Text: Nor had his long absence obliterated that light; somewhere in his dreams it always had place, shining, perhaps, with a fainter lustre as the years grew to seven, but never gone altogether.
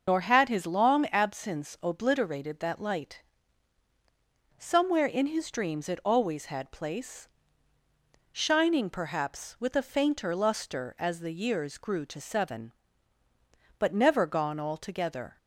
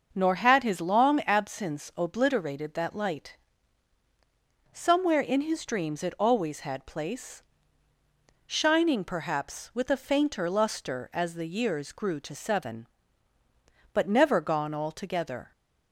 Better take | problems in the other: second | loses the start of "Nor"; at 0.0 s; 115 ms // starts louder than the rest; noticeable; until 1.0 s; 6 dB; noticeable in the second

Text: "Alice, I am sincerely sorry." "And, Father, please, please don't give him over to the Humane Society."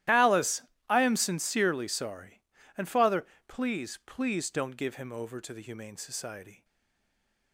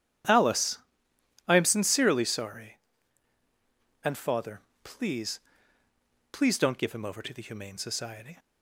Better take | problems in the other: second | starts louder than the rest; strong; until 1.3 s; 14 dB; strong in the second // stays silent after the last word; slight; from 6.6 s on; 0.9 s long

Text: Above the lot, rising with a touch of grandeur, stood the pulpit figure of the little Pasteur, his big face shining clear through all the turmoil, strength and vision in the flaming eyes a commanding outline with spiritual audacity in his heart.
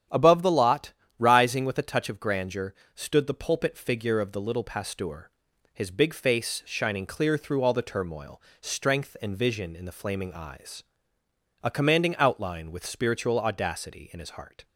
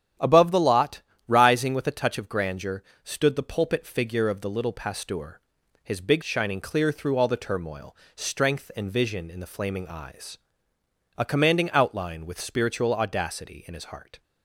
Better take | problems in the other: first | starts louder than the rest; strong; until 1.4 s; 10 dB; strong in the first // skips "face"; at 6.2 s // pauses between "eyes" and "a"; noticeable; at 10.3 s; 0.80 s long; noticeable in the first

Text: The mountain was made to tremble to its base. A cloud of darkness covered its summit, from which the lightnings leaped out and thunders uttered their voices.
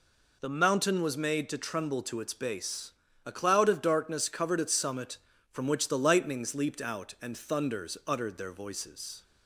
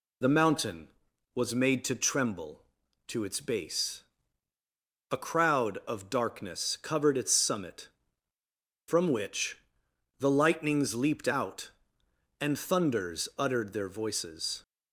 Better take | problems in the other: first | says "crowd" for "cloud"; at 5.1 s // pauses between "which" and "the"; noticeable; at 9.5 s; 0.60 s long

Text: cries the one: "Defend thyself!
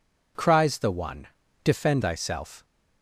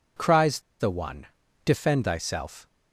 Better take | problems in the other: first | pauses between "cries" and "the"; slight; at 0.5 s; 0.20 s long

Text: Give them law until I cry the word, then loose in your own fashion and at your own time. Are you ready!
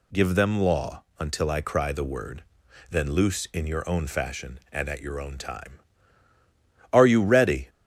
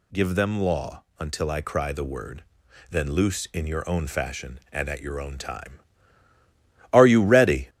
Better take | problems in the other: first | gets louder; throughout; 4 dB // pauses between "law" and "until"; slight; at 1.0 s; 0.16 s long; slight in the first

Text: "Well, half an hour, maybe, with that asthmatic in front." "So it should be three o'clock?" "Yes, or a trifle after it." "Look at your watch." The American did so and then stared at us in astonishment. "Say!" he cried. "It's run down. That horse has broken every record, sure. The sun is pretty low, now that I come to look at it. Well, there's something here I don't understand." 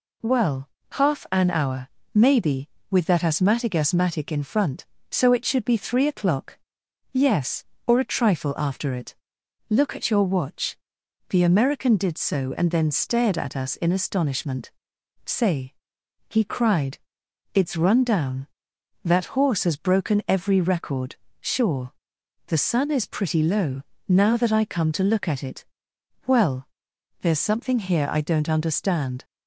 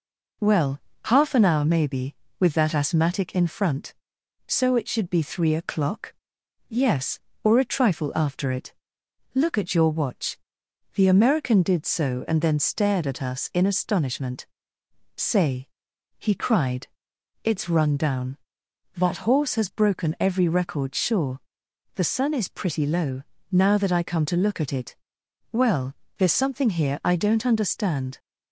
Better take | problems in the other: second | says "asthmatic" twice; at 3.7 s

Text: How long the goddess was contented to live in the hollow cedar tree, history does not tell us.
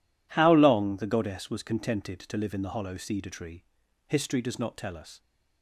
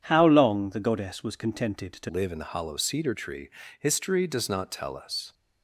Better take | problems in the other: first | starts louder than the rest; strong; until 1.0 s; 8.5 dB // changes voice at "live"; from 2.0 s on; 3.3 s long

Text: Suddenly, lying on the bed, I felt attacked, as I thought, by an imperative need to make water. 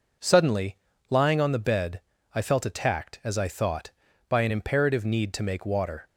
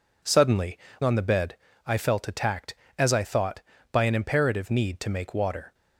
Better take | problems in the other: first | skips "lying"; at 0.9 s

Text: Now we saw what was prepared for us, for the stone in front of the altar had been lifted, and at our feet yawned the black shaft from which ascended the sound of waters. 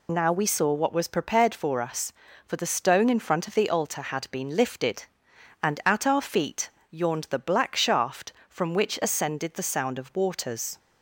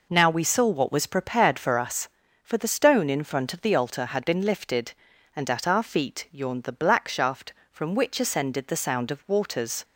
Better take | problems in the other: second | loses the start of "Now"; at 0.0 s; 30 ms // pauses between "feet" and "yawned"; slight; at 6.6 s; 0.22 s long

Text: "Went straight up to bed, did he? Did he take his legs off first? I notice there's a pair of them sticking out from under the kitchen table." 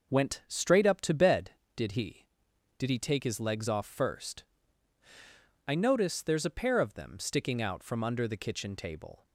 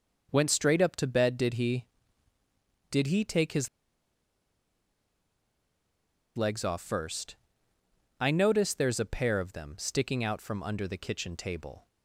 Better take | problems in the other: first | pauses between "his" and "legs"; strong; at 3.6 s; 2.6 s long

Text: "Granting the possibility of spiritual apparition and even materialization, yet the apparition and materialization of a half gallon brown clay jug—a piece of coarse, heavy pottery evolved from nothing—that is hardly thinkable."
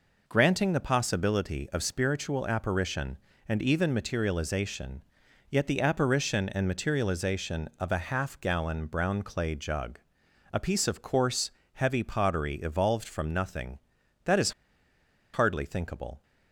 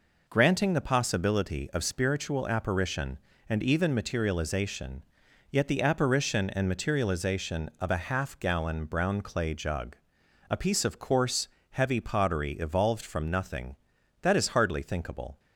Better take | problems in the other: second | pauses between "is" and "hardly"; noticeable; at 14.5 s; 0.81 s long

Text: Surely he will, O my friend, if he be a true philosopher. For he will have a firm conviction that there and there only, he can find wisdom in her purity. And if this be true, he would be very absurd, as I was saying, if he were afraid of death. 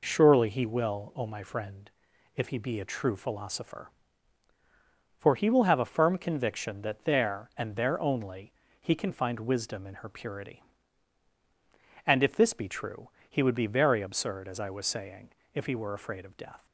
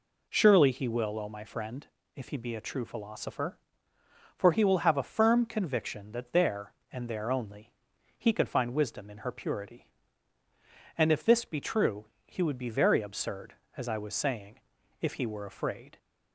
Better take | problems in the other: first | stops before "of death"; at 15.9 s

